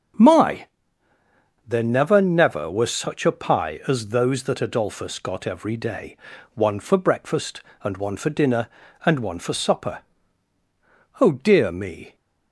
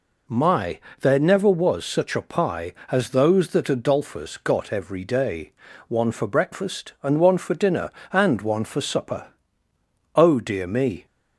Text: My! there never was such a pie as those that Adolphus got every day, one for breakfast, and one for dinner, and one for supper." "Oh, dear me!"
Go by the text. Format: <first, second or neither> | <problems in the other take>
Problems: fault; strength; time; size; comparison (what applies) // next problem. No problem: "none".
second | starts louder than the rest; strong; until 2.1 s; 7.5 dB // says "never" twice; at 2.2 s